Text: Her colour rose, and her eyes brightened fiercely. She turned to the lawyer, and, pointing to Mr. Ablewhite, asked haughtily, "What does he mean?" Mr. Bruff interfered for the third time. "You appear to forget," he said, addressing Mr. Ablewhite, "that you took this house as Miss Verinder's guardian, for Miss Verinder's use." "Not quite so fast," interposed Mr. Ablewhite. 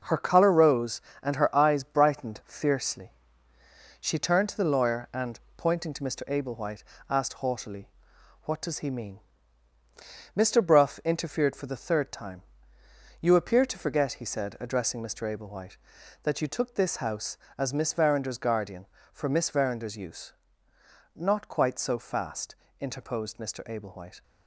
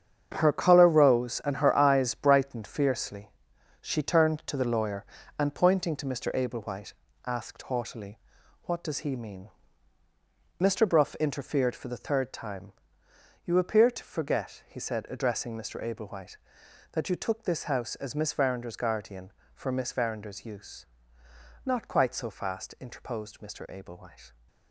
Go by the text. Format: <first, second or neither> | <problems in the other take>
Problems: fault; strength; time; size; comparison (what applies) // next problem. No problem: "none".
first | gets quieter; strong; throughout; 10.5 dB